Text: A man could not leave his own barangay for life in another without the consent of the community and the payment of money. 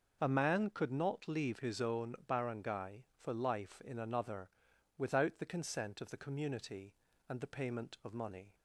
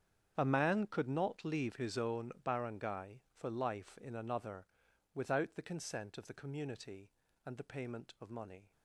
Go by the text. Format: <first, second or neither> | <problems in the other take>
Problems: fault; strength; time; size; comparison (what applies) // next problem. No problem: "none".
first | gets quieter; strong; throughout; 16.5 dB // starts louder than the rest; strong; until 1.3 s; 8.5 dB; also in the first // pauses between "another" and "without"; noticeable; at 4.6 s; 0.48 s long; noticeable in the first